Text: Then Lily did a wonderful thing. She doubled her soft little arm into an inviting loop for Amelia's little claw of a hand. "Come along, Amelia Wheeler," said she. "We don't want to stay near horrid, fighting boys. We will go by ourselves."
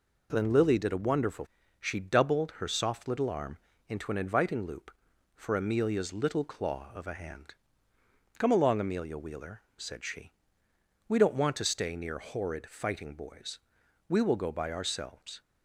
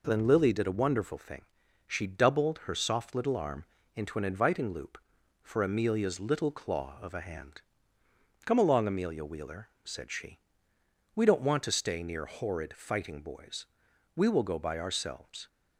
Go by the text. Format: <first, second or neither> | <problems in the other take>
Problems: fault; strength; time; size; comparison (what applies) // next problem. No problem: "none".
second | skips "thing"; at 1.6 s // pauses between "arm" and "into"; slight; at 3.5 s; 0.32 s long; slight in the second